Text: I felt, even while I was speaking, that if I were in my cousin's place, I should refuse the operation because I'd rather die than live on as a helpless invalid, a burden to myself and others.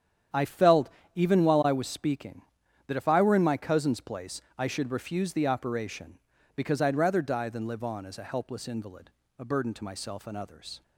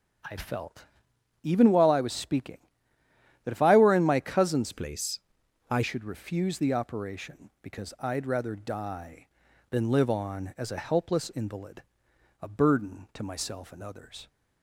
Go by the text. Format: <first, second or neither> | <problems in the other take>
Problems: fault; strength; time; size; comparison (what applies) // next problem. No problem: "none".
first | starts louder than the rest; strong; until 1.8 s; 7.5 dB; strong in the first // changes voice from "place" to "I"; from 4.7 to 5.8 s; 1.1 s long